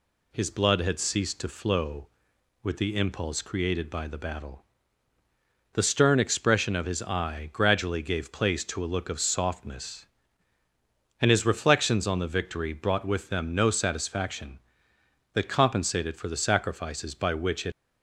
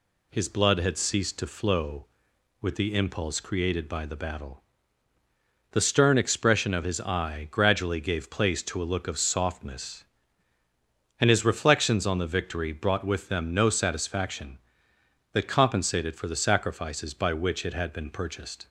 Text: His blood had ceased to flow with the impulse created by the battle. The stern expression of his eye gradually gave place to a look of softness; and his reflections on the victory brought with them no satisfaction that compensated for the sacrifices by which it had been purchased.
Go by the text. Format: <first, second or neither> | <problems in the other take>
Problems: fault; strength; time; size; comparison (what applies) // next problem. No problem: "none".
second | stops before "had been purchased"; at 17.7 s